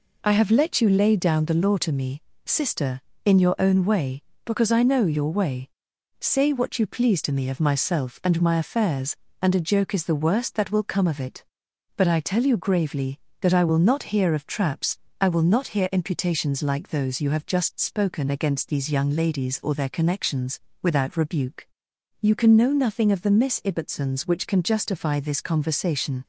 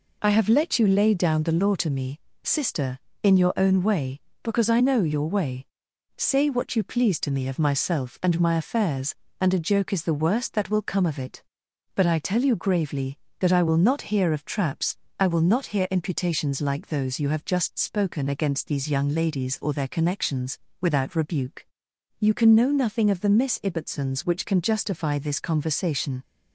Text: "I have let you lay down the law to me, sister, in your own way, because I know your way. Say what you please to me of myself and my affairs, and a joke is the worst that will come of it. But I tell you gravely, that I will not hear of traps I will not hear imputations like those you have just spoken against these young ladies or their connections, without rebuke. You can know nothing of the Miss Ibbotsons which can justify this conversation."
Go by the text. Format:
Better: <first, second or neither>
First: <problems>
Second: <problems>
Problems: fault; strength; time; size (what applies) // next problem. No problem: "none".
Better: neither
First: pauses between "traps" and "I"; slight; at 14.9 s; 0.24 s long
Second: pauses between "traps" and "I"; slight; at 14.9 s; 0.24 s long